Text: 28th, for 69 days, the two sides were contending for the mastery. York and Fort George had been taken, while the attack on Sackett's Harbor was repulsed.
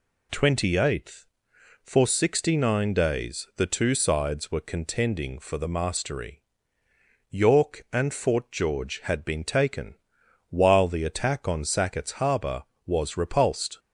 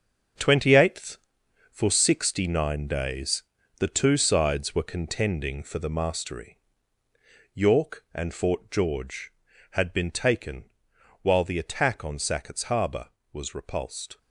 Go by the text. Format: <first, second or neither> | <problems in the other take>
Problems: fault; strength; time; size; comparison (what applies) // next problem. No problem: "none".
first | gets quieter; strong; throughout; 9.5 dB